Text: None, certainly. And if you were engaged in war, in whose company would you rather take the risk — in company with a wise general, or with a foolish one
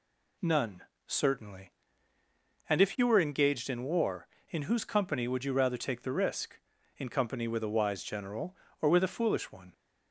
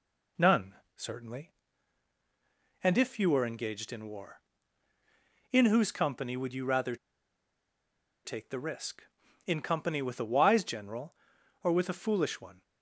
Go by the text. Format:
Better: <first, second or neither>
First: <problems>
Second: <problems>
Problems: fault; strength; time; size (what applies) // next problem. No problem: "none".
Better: first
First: none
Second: pauses between "rather" and "take"; strong; at 6.9 s; 1.2 s long